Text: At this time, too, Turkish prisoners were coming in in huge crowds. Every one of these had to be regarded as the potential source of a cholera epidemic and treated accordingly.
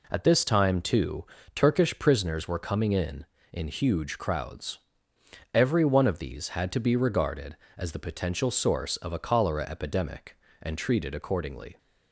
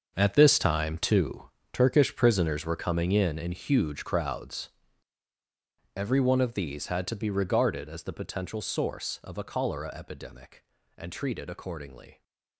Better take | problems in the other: first | gets quieter; strong; throughout; 12.5 dB

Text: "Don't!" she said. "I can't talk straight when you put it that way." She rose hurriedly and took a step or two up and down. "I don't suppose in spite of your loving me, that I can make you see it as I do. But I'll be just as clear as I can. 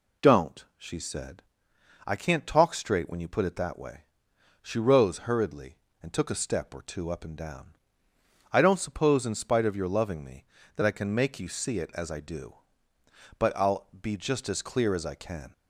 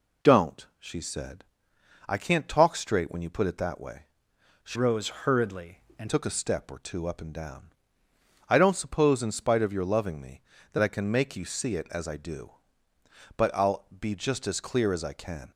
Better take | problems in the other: first | changes voice from "rose" to "and"; from 4.7 to 6.0 s; 1.3 s long // pauses between "rose" and "hurriedly"; slight; at 5.0 s; 0.16 s long

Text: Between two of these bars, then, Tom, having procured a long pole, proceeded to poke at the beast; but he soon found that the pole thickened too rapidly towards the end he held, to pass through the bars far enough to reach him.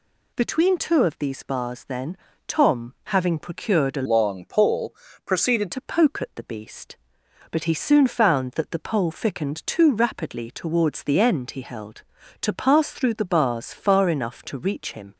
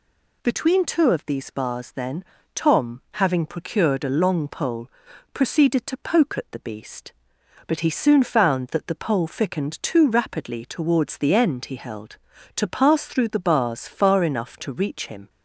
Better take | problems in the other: second | changes voice from "long" to "proceeded"; from 4.0 to 5.7 s; 1.7 s long

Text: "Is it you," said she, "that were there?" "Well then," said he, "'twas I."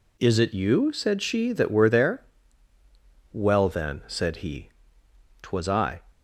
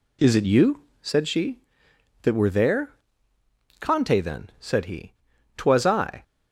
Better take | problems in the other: first | says "Conte" for "Well"; at 3.7 s

